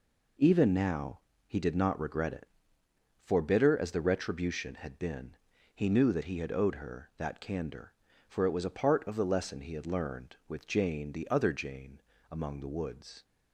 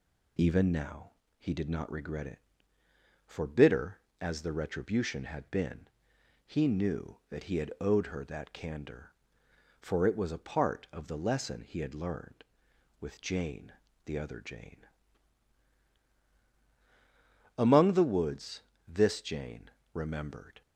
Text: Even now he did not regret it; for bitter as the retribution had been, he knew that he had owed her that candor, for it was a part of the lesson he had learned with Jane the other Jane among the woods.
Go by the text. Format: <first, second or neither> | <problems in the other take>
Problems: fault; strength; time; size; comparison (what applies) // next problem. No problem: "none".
first | pauses between "now" and "he"; slight; at 1.1 s; 0.26 s long; slight in the first // pauses between "Jane" and "the"; slight; at 13.7 s; 0.34 s long // pauses between "Jane" and "among"; strong; at 14.8 s; 2.7 s long; slight in the first // goes on to say "This Jane remembered"; strong; from 18.8 s on; 1.7 s long